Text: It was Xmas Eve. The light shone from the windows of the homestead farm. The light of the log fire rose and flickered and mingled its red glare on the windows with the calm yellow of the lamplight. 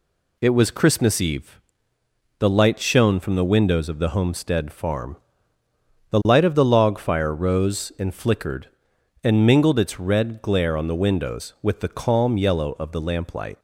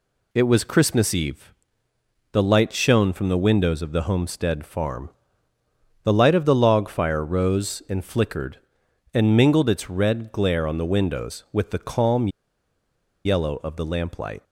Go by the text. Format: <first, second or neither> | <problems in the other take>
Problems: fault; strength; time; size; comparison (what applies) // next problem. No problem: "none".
first | pauses between "calm" and "yellow"; noticeable; at 12.2 s; 0.96 s long